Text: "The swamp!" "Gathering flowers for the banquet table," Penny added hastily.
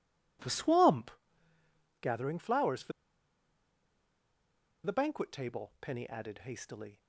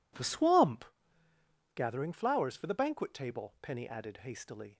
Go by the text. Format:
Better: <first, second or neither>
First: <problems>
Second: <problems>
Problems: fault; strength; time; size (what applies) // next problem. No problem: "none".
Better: second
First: pauses between "for" and "the"; strong; at 2.9 s; 1.9 s long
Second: none